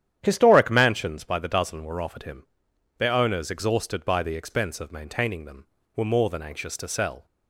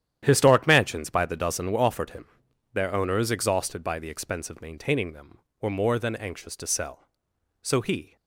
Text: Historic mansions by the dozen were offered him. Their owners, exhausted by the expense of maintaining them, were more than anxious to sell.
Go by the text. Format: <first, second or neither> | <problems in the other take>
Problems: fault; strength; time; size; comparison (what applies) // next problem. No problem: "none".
first | starts louder than the rest; strong; until 1.2 s; 10.5 dB; strong in the first // goes on to say "So he"; from 7.6 s on; 0.54 s long